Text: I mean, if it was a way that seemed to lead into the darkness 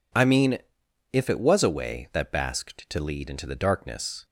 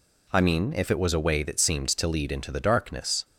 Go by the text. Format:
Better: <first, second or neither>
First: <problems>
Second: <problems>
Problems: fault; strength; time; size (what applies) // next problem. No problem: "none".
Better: second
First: says "basked" for "seemed"; at 2.3 s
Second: none